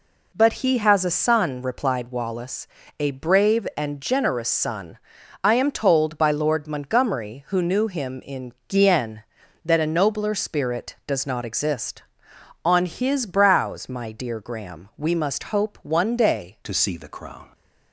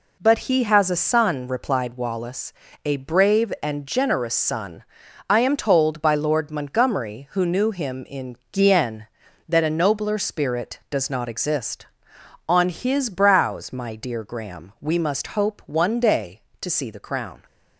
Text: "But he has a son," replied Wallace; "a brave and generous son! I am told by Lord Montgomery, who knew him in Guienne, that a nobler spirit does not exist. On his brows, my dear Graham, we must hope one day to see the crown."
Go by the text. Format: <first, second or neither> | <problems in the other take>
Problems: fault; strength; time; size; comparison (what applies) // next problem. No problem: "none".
second | pauses between "in" and "Guienne"; slight; at 8.5 s; 0.16 s long; slight in the second // changes voice at "to"; from 16.6 s on; 0.9 s long